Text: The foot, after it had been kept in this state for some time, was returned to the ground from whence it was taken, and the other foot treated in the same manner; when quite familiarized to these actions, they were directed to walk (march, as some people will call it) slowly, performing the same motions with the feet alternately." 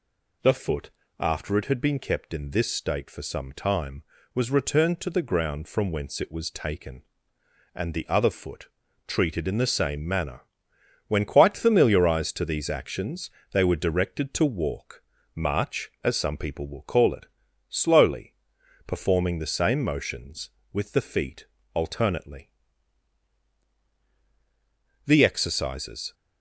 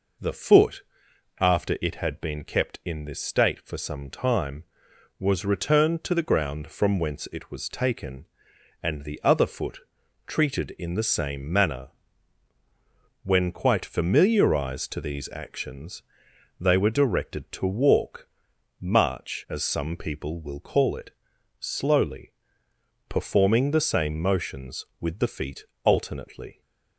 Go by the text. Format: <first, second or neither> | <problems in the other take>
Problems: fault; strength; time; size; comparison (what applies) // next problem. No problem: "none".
second | pauses between "foot" and "treated"; slight; at 8.6 s; 0.36 s long; noticeable in the second // pauses between "feet" and "alternately"; slight; at 21.4 s; 0.26 s long; slight in the second // goes on to say "The exercises"; noticeable; from 25.0 s on; 1.1 s long